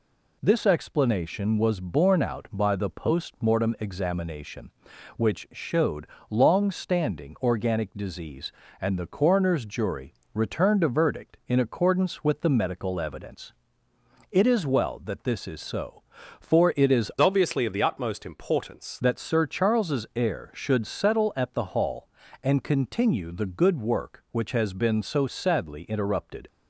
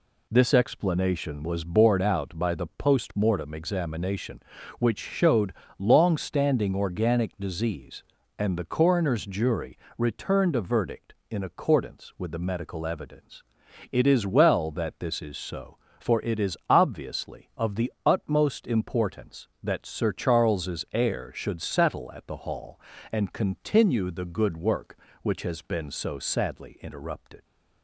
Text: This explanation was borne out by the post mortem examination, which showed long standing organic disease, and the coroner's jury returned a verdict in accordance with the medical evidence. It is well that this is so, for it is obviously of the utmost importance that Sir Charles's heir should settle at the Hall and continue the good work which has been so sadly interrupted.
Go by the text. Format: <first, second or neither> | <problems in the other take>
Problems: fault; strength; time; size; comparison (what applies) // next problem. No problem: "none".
second | pauses between "showed" and "long"; slight; at 6.0 s; 0.22 s long; slight in the second // pauses between "jury" and "returned"; slight; at 10.1 s; 0.20 s long; slight in the second // changes voice from "obviously" to "importance"; from 17.2 to 18.9 s; 1.7 s long